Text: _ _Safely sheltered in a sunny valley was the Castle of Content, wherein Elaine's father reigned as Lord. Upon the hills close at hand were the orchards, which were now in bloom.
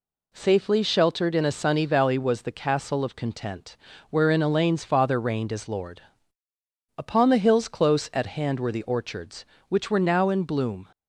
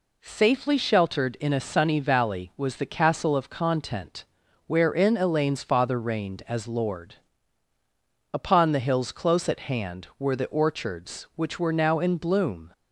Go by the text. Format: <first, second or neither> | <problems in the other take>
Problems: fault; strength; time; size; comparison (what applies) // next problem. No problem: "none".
neither | none